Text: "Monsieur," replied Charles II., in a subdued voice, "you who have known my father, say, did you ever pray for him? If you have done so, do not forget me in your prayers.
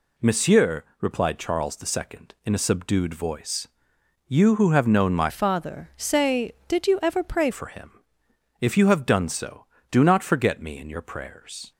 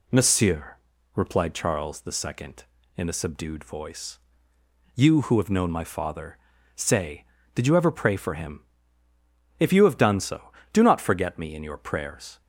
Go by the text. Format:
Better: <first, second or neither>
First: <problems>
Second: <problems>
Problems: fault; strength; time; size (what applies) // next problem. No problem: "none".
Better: second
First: changes voice from "father" to "pray"; from 5.2 to 7.5 s; 2.3 s long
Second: none